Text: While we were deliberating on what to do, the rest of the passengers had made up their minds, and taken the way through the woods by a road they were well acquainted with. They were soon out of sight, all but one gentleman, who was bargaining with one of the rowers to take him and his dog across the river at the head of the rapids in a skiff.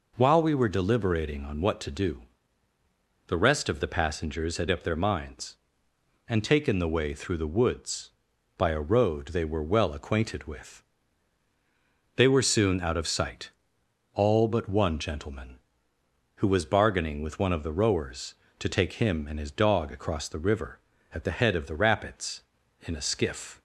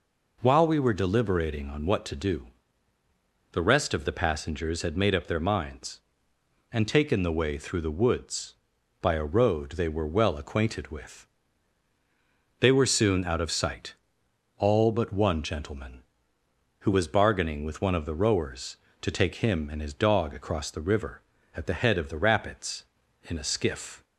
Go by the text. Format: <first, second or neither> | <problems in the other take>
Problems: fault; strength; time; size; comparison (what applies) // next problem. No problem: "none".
second | skips "made"; at 4.6 s